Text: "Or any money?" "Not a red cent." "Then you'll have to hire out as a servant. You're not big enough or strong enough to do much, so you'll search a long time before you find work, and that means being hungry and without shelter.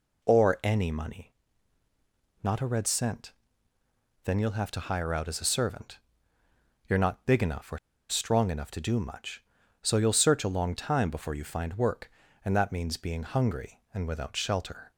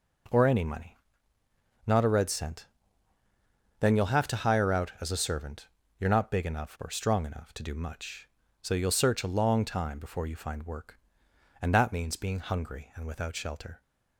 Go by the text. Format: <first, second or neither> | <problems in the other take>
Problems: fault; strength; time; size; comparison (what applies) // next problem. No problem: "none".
second | pauses between "or" and "strong"; slight; at 7.7 s; 0.31 s long